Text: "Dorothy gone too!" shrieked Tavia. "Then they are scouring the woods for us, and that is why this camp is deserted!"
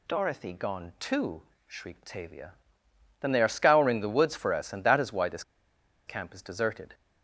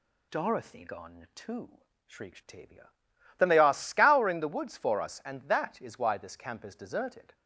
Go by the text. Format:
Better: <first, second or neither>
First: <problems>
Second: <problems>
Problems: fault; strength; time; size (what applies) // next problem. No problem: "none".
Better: second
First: pauses between "this" and "camp"; noticeable; at 5.4 s; 0.64 s long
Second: none